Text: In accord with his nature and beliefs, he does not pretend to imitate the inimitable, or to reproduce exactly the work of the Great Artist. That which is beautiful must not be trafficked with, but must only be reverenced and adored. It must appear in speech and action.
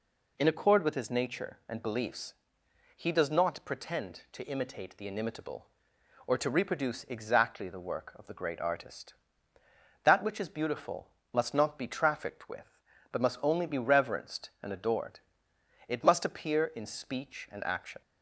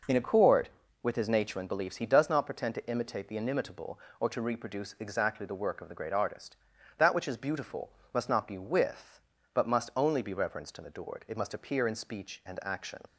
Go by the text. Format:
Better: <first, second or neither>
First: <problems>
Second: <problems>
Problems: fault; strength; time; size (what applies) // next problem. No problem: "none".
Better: first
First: pauses between "beautiful" and "must"; slight; at 11.0 s; 0.26 s long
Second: pauses between "beautiful" and "must"; slight; at 7.8 s; 0.24 s long // skips "trafficked"; at 8.5 s